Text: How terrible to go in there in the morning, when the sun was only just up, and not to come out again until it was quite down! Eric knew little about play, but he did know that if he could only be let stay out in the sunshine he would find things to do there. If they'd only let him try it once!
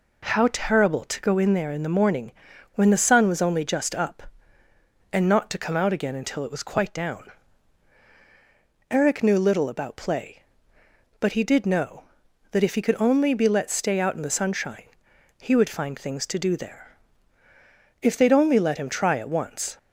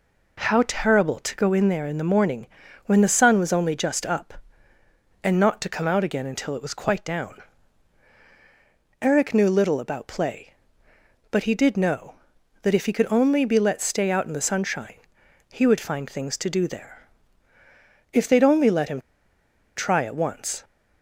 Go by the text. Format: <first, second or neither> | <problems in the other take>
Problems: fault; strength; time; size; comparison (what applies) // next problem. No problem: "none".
first | pauses between "sunshine" and "he"; noticeable; at 14.9 s; 0.58 s long; noticeable in the first // pauses between "him" and "try"; noticeable; at 19.0 s; 0.76 s long